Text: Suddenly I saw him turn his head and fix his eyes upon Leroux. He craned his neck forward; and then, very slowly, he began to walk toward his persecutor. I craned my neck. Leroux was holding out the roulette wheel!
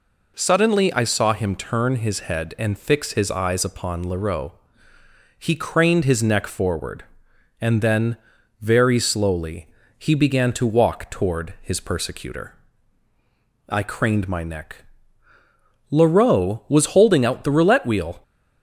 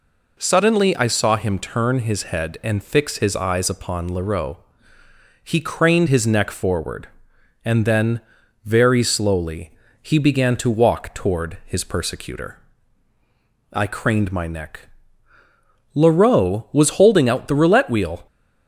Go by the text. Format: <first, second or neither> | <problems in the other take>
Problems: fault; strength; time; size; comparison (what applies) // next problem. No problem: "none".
neither | none